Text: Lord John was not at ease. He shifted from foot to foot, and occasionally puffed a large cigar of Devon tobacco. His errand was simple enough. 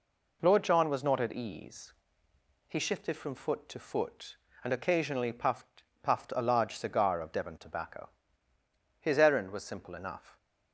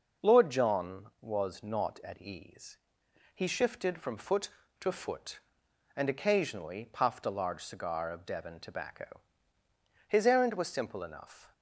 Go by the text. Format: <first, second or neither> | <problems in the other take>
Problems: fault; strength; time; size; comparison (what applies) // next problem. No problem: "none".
second | says "puffed" twice; at 6.0 s